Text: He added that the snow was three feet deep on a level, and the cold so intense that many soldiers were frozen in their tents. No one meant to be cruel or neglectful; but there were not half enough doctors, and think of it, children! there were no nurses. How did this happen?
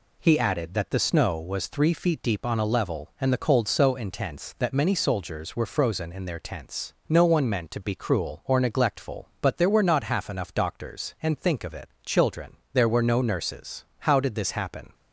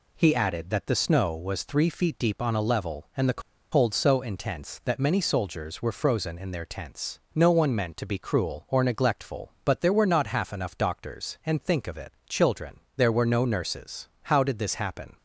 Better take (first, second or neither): first